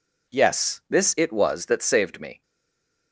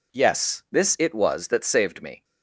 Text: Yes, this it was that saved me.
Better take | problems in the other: second | stays silent after the last word; slight; from 2.4 s on; 0.7 s long

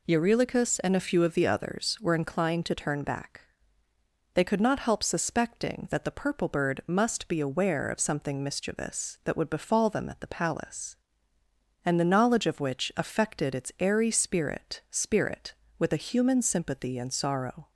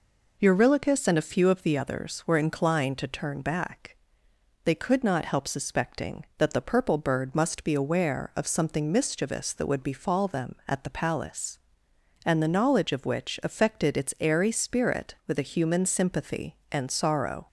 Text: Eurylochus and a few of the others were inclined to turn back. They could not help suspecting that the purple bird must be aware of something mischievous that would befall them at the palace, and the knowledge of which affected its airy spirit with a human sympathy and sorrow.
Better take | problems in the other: second | says "spirit" twice; at 14.9 s

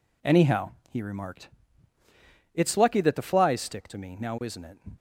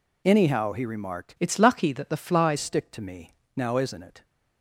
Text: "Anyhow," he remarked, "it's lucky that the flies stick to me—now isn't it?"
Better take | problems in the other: first | changes voice from "it's" to "flies"; from 1.3 to 2.5 s; 1.2 s long

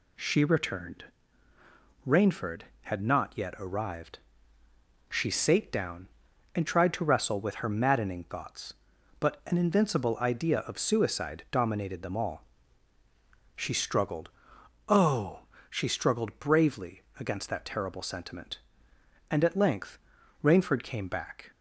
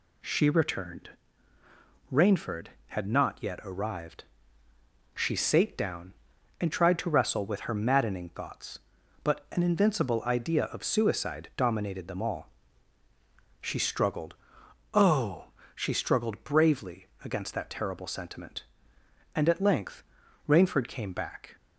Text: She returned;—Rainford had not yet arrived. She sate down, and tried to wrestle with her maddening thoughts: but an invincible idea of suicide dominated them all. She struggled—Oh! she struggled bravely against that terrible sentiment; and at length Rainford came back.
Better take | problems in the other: neither | pauses between "bravely" and "against"; slight; the same in both // pauses between "length" and "Rainford"; the same in both

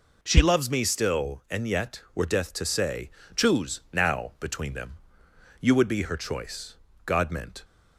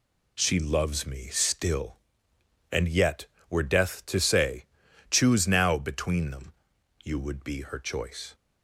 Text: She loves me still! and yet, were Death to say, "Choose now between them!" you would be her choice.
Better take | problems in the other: second | goes on to say "God meant"; from 7.0 s on; 0.58 s long

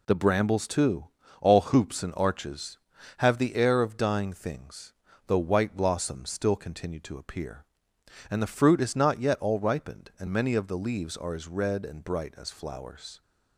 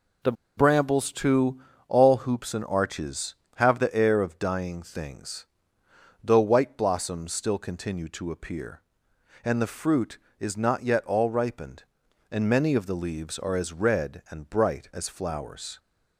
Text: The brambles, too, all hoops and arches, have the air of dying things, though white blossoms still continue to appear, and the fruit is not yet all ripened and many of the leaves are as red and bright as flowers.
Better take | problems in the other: first | pauses between "The" and "brambles"; slight; at 0.3 s; 0.24 s long

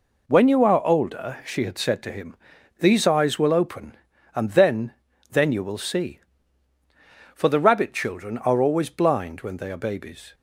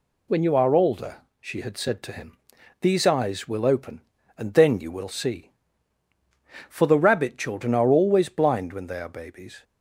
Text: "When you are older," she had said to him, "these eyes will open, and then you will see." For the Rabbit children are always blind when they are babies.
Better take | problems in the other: second | says "then" twice; at 5.2 s

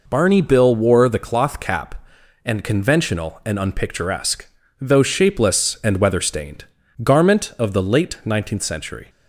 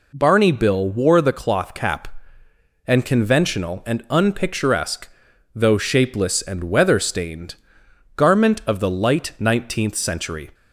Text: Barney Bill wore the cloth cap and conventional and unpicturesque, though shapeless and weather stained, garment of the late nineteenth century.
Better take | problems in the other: first | says "light" for "late"; at 8.9 s

